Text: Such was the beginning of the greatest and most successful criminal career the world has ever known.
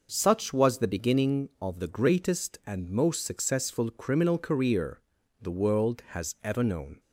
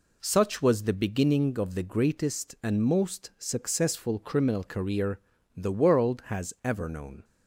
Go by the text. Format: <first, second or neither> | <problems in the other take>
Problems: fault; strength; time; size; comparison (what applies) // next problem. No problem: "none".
neither | pauses between "career" and "the"; the same in both